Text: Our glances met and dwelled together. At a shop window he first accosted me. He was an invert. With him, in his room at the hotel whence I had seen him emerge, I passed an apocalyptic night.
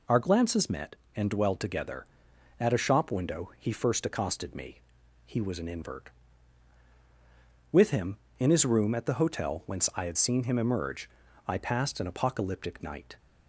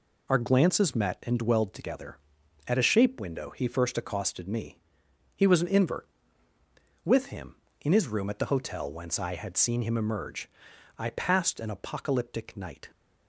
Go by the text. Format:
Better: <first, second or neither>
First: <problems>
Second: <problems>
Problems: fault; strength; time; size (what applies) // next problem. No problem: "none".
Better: first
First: none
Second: says "shape" for "shop"; at 2.8 s